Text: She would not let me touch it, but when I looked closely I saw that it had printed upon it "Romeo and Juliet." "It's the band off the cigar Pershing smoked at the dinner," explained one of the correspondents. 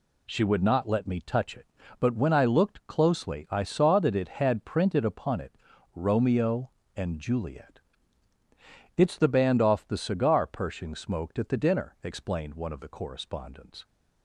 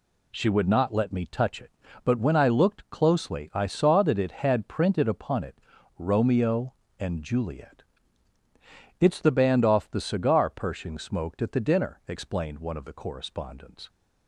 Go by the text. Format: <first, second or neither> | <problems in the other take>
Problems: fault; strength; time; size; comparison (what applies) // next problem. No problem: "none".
neither | pauses between "it" and "Romeo"; the same in both